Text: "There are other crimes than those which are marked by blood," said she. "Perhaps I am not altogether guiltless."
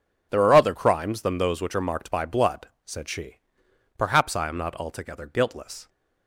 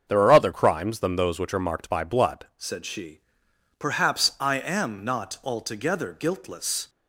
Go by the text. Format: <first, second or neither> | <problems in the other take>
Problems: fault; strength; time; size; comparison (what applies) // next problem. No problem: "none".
first | starts louder than the rest; until 1.0 s; 6.5 dB // changes voice at "said"; from 2.5 s on; 4.3 s long